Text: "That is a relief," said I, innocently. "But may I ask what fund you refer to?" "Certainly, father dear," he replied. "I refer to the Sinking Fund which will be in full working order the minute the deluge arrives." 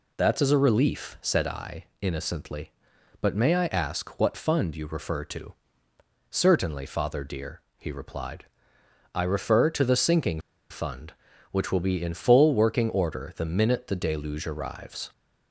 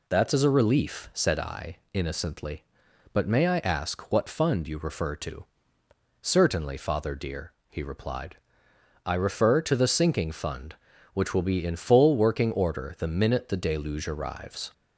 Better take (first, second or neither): second